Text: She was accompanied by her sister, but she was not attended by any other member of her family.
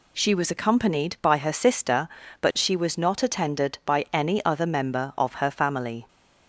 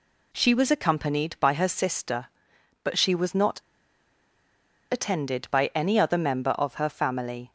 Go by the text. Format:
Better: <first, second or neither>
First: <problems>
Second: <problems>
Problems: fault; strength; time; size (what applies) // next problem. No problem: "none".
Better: first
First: none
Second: pauses between "not" and "attended"; strong; at 3.5 s; 1.3 s long